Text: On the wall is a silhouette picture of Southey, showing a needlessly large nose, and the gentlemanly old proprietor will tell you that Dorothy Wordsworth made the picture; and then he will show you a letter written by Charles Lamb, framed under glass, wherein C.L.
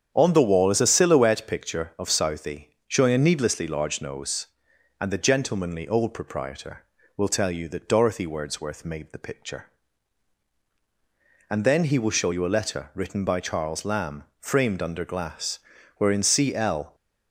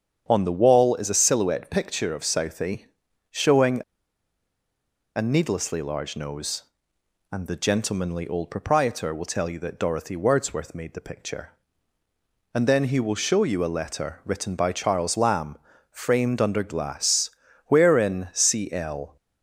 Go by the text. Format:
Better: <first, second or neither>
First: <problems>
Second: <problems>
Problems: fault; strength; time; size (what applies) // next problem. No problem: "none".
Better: first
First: starts louder than the rest; strong; until 1.1 s; 8.5 dB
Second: starts louder than the rest; strong; until 1.3 s; 8 dB // pauses between "showing" and "a"; strong; at 3.8 s; 1.3 s long